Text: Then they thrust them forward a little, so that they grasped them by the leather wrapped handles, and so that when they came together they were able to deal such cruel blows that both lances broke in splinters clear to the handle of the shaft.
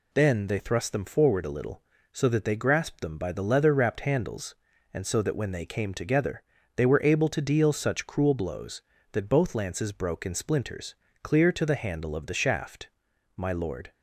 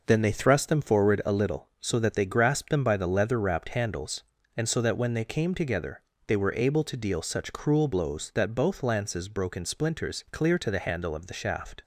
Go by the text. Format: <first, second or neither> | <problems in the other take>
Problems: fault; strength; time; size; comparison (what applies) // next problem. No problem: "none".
second | pauses between "together" and "they"; slight; at 6.4 s; 0.34 s long; slight in the second // pauses between "splinters" and "clear"; slight; at 10.9 s; 0.26 s long // goes on to say "My lord"; from 13.3 s on; 0.56 s long